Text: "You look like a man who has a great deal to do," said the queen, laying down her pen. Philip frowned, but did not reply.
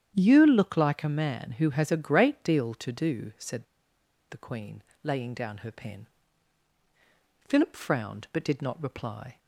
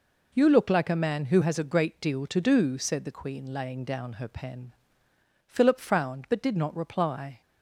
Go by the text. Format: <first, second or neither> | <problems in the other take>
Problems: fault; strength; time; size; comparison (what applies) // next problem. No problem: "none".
second | starts louder than the rest; strong; until 1.1 s; 9.5 dB // pauses between "said" and "the"; noticeable; at 3.6 s; 0.65 s long